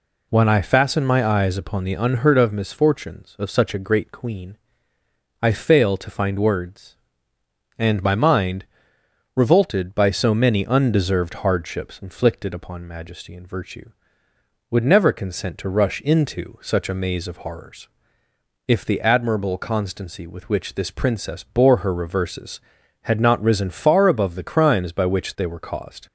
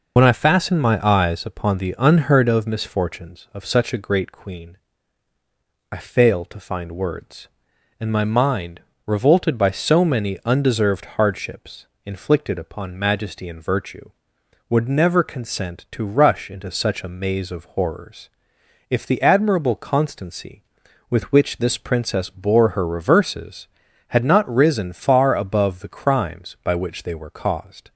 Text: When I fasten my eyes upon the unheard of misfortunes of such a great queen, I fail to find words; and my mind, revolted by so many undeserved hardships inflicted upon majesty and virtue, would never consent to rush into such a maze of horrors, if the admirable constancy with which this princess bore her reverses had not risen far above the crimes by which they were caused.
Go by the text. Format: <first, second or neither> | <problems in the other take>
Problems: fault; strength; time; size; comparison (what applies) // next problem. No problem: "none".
first | loses the start of "When"; at 0.1 s; 45 ms // pauses between "hardships" and "inflicted"; slight; at 11.8 s; 0.18 s long